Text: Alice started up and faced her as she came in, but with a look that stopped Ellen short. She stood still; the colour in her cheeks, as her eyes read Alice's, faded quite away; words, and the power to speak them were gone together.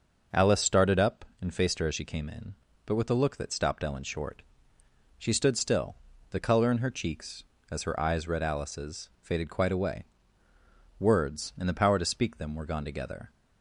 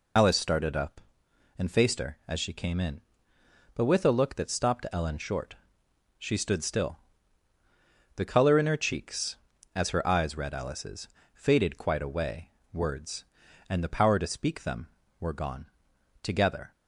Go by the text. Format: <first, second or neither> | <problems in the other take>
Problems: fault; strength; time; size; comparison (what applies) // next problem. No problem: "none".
first | loses the start of "Alice"; at 0.1 s; 65 ms // pauses between "gone" and "together"; noticeable; at 15.6 s; 0.56 s long